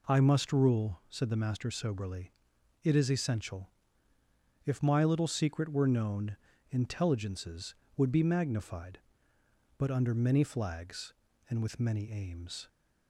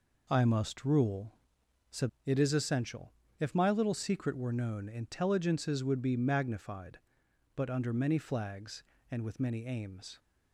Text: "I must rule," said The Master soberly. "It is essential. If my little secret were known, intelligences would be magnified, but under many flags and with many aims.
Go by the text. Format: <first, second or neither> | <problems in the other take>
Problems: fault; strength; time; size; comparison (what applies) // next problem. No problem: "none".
first | skips "The Master soberly"; at 2.1 s